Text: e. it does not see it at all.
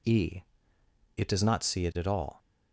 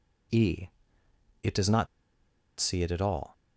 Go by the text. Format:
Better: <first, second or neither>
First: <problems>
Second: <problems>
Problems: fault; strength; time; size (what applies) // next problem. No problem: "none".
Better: first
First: none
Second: pauses between "not" and "see"; noticeable; at 1.8 s; 0.72 s long